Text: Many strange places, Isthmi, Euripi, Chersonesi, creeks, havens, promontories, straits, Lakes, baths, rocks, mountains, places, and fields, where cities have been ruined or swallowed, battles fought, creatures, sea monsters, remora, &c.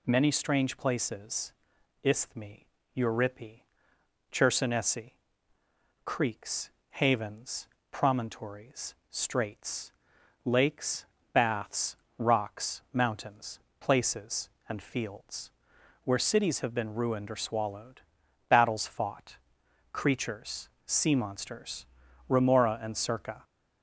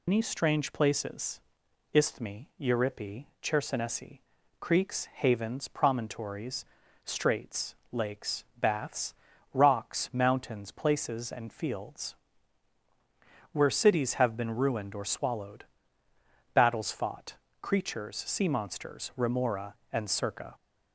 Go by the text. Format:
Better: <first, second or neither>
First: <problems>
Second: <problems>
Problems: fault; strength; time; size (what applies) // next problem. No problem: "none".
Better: first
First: none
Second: loses the start of "Many"; at 0.0 s; 130 ms